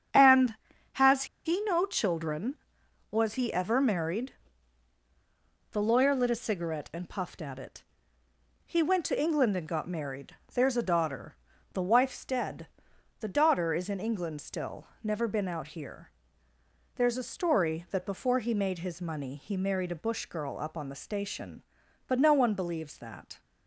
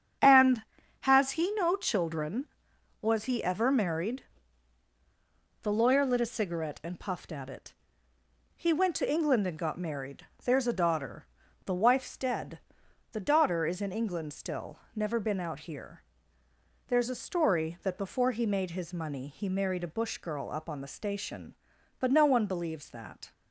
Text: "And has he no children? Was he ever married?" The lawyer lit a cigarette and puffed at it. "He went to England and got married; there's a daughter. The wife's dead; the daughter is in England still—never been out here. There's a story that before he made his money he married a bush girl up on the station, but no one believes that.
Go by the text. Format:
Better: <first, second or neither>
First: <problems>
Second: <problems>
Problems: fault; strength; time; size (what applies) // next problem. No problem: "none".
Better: second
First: starts louder than the rest; strong; until 1.7 s; 8 dB // pauses between "has" and "he"; slight; at 1.2 s; 0.20 s long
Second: starts louder than the rest; strong; until 1.5 s; 7.5 dB